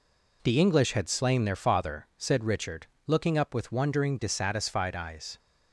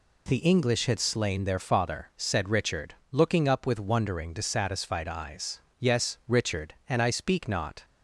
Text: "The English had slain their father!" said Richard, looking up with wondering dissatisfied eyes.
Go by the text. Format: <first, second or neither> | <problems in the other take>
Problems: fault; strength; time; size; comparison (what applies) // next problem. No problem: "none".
first | goes on to say "Yes Richard and I speak not"; strong; from 5.7 s on; 2.0 s long